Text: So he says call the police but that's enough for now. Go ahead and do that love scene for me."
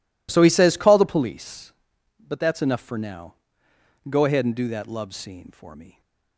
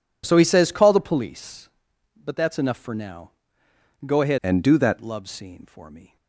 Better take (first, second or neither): first